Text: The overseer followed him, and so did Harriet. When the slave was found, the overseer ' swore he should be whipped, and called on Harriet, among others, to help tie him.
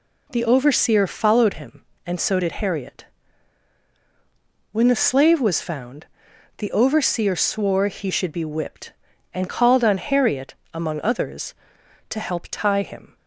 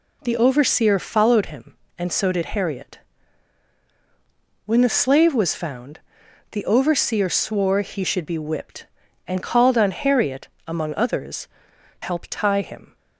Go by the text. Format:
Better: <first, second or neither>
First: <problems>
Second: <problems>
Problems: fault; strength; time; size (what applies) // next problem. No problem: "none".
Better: first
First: none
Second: skips "to"; at 11.7 s